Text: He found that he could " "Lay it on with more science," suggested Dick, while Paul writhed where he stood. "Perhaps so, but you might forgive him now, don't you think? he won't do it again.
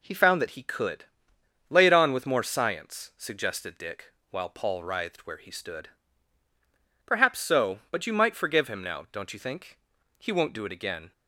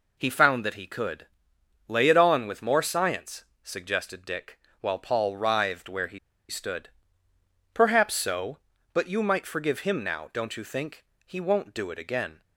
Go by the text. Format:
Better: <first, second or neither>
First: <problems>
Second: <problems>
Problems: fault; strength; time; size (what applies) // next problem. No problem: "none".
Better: first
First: none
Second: pauses between "he" and "stood"; slight; at 6.1 s; 0.30 s long